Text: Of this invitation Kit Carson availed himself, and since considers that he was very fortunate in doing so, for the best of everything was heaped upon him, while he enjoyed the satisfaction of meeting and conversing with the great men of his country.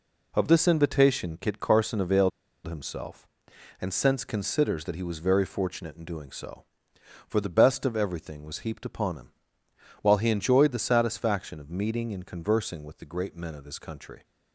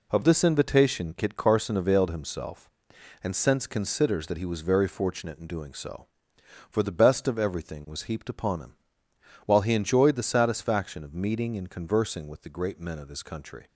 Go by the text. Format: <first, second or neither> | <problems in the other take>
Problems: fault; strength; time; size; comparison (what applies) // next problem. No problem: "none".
second | pauses between "availed" and "himself"; at 2.3 s; 0.36 s long